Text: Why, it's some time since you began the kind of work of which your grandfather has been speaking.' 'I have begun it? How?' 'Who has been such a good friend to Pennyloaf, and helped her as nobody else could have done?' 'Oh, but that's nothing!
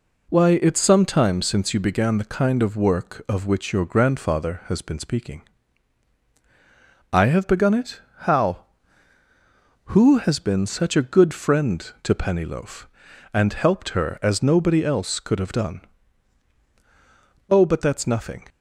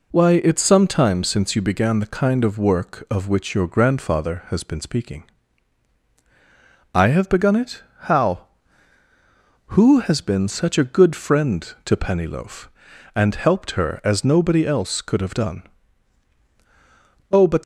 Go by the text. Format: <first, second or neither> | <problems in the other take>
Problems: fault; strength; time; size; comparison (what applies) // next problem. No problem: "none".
first | stops before "that's nothing"; at 17.6 s